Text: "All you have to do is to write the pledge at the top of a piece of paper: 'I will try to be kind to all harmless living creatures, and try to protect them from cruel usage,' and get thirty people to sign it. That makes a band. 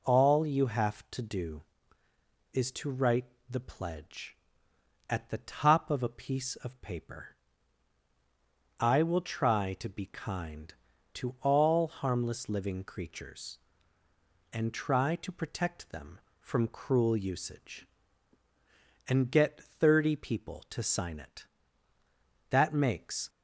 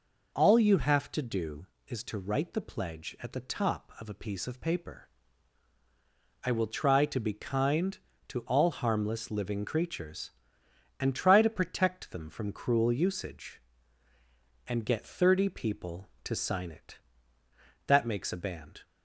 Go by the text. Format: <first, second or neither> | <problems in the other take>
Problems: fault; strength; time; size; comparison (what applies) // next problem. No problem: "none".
second | pauses between "write" and "the"; slight; at 3.2 s; 0.20 s long // stops before "a band"; at 23.2 s